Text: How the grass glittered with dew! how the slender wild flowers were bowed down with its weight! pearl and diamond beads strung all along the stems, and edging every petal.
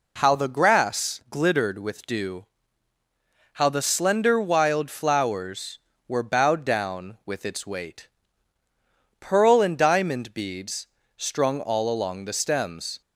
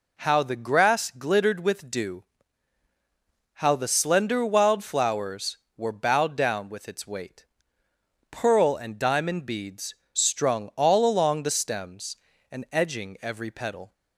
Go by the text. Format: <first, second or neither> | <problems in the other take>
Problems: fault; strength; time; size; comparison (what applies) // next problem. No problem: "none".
second | pauses between "beads" and "strung"; slight; at 10.8 s; 0.32 s long; slight in the second // stops before "and edging every petal"; at 13.0 s